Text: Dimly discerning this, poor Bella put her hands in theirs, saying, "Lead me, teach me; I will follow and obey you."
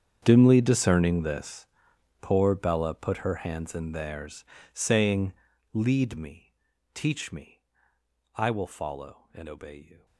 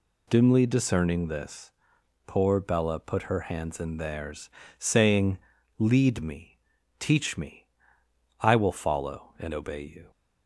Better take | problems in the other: second | gets quieter; strong; throughout; 20 dB

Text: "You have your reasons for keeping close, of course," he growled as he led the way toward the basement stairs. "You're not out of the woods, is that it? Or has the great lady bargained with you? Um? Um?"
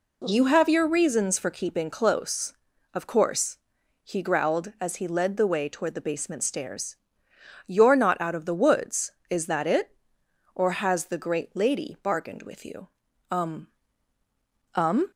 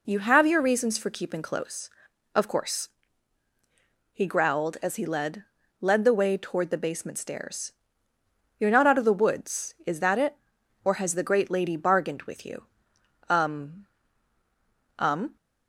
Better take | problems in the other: first | says "led" twice; at 5.7 s

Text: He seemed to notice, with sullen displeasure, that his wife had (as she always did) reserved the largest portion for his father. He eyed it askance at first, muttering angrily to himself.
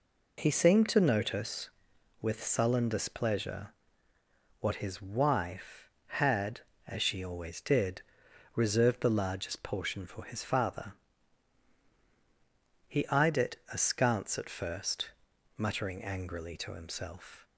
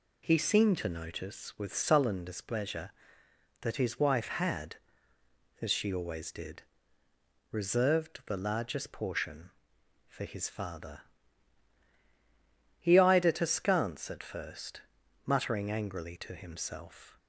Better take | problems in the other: second | says "what" for "that"; at 4.6 s // pauses between "it" and "askance"; slight; at 13.5 s; 0.16 s long

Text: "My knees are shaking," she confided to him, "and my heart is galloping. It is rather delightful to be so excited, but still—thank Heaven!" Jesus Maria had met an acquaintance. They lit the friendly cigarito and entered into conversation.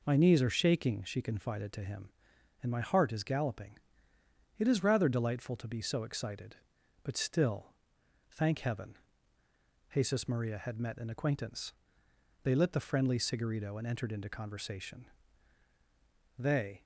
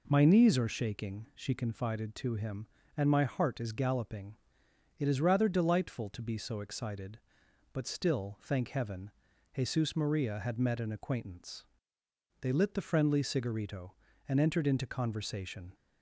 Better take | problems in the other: second | goes on to say "They"; slight; from 16.3 s on; 0.46 s long

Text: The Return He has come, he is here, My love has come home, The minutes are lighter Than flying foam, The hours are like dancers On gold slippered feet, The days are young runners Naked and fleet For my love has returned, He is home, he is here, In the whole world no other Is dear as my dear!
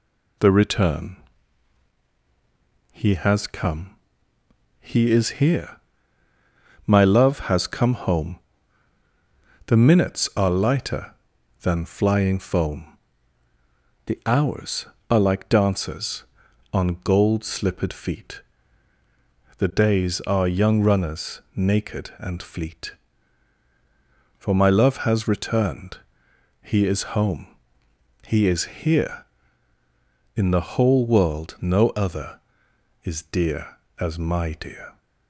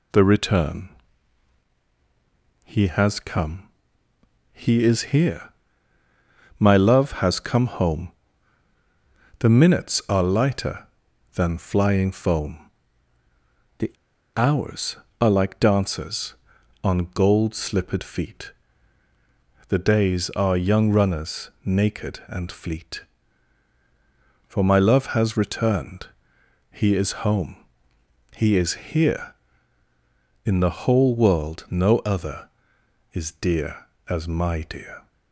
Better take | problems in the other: first | pauses between "Return" and "He"; strong; at 0.8 s; 1.7 s long; strong in the first // pauses between "The" and "hours"; at 13.9 s; 0.43 s long

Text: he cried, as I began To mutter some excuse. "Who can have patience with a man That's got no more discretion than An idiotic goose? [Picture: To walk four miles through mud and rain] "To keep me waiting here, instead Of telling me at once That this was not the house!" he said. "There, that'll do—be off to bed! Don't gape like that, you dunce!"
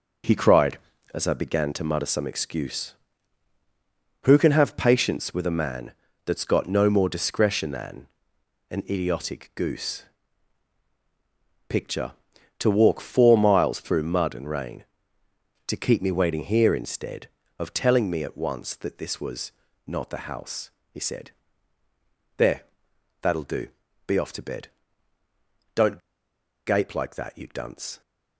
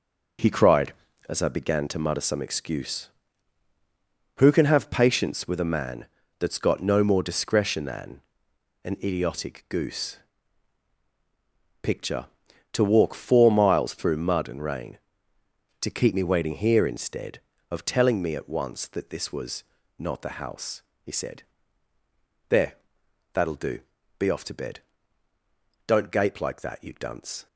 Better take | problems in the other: second | pauses between "man" and "That's"; slight; at 5.9 s; 0.32 s long; slight in the second // pauses between "than" and "An"; noticeable; at 8.0 s; 0.64 s long; noticeable in the second // pauses between "was" and "not"; slight; at 19.5 s; 0.34 s long; slight in the second // pauses between "Don't" and "gape"; noticeable; at 25.9 s; 0.67 s long

